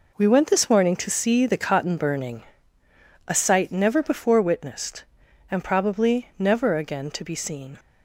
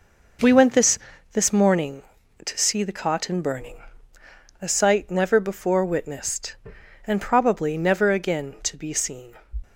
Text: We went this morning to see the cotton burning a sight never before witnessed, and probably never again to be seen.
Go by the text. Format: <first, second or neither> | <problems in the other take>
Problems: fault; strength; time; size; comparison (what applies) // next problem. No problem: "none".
first | says "this" twice; at 1.3 s // pauses between "burning" and "a"; noticeable; at 3.7 s; 0.86 s long; noticeable in the first